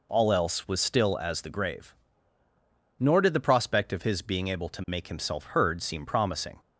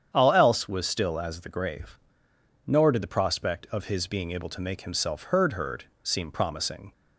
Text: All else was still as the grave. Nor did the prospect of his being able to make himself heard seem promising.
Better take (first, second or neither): first